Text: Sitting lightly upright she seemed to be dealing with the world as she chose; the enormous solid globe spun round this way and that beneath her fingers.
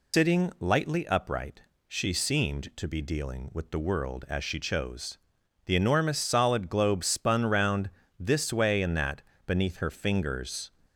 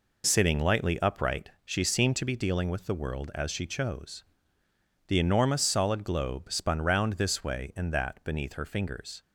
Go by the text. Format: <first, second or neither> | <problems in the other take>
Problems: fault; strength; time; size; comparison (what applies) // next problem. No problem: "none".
second | loses the start of "Sitting"; at 0.1 s; 125 ms // pauses between "upright" and "she"; slight; at 1.6 s; 0.28 s long // pauses between "round" and "this"; slight; at 7.8 s; 0.30 s long // pauses between "that" and "beneath"; slight; at 9.2 s; 0.24 s long